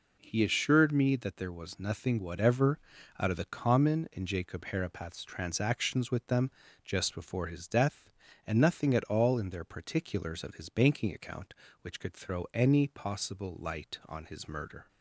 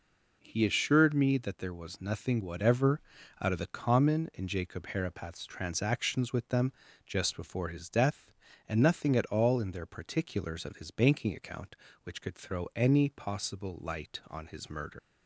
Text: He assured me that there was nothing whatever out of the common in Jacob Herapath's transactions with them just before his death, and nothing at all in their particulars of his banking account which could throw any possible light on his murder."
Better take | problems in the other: first | pauses between "whatever" and "out"; at 2.9 s; 0.40 s long; also in the first // pauses between "them" and "just"; slight; at 6.7 s; 0.34 s long; slight in the first // leaves "murder" unfinished; at 14.9 s; 100 ms

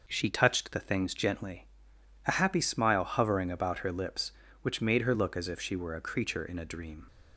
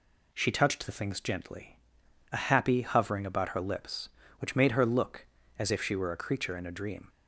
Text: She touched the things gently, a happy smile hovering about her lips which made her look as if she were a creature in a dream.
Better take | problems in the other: first | skips "smile"; at 2.8 s

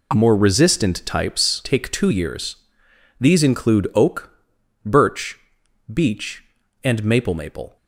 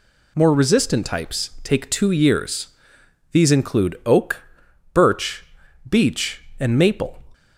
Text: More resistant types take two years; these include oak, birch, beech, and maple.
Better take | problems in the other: second | says "maple" twice; at 7.3 s

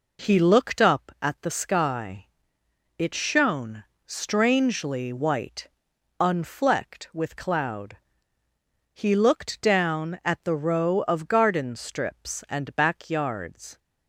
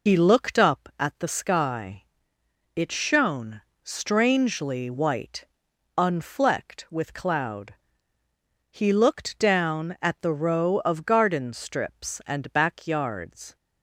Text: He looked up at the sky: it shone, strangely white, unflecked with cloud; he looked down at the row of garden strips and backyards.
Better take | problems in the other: first | loses the start of "He"; at 0.0 s; 95 ms

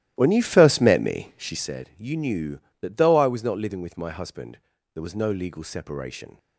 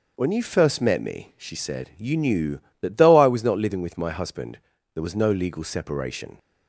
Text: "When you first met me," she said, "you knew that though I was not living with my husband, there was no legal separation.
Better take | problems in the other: second | starts louder than the rest; strong; until 1.8 s; 14 dB

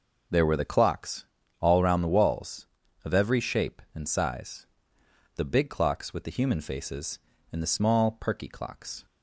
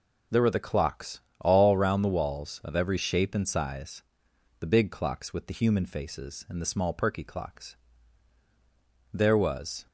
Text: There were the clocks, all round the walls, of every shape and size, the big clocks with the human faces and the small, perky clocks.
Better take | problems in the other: first | goes on to say "There was"; noticeable; from 9.1 s on; 0.74 s long

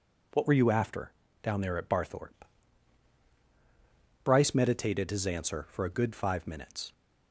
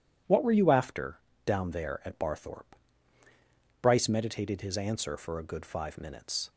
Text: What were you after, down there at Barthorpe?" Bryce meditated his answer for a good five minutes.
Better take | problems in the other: neither | none

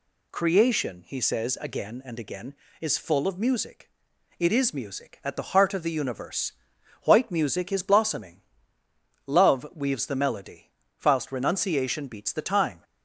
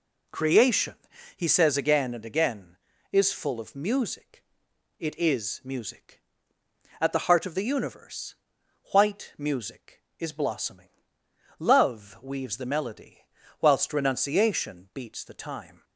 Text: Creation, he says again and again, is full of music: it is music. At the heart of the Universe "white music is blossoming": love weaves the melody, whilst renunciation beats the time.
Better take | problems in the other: neither | pauses between "Universe" and "white"; noticeable; the same in both

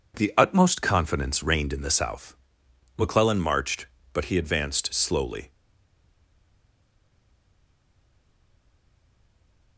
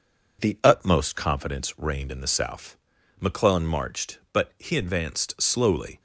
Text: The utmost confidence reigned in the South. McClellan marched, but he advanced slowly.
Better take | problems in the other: second | stays silent after the last word; strong; from 5.4 s on; 4.3 s long

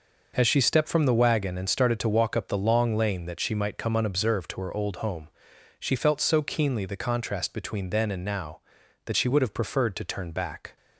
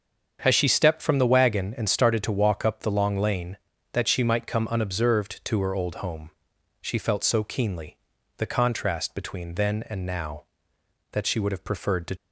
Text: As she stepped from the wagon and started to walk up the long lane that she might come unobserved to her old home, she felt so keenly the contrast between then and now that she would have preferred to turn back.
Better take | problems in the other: first | starts louder than the rest; until 1.4 s; 7 dB // pauses between "keenly" and "the"; at 7.9 s; 0.40 s long // stops before "turn back"; at 12.1 s

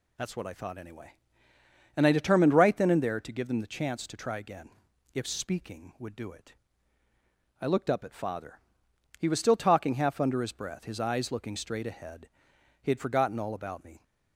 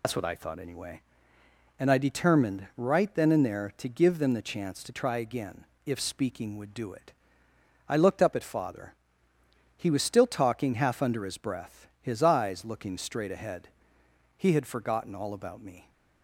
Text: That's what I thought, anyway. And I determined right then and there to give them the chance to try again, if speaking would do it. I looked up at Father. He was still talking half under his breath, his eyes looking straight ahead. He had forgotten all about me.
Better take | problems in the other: first | loses the start of "That's"; at 0.0 s; 105 ms

